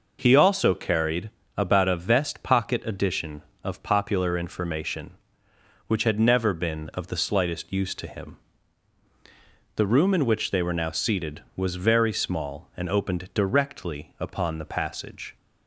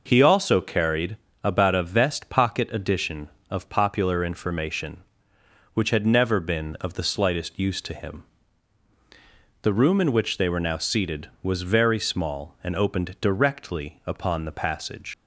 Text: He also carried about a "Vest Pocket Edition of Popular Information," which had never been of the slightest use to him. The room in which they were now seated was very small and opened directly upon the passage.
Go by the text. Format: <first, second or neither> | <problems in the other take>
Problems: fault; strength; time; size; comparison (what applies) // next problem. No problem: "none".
first | pauses between "carried" and "about"; slight; at 1.1 s; 0.26 s long; slight in the first // leaves "passage" unfinished; at 15.1 s; 85 ms